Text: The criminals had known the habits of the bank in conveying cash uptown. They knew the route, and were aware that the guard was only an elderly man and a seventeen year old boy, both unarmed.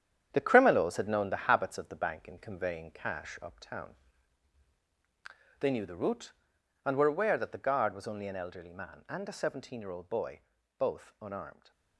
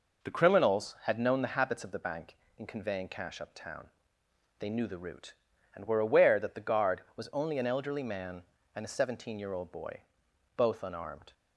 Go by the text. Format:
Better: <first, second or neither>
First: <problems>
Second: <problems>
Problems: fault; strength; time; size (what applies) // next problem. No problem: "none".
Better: second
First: gets quieter; strong; throughout; 7.5 dB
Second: none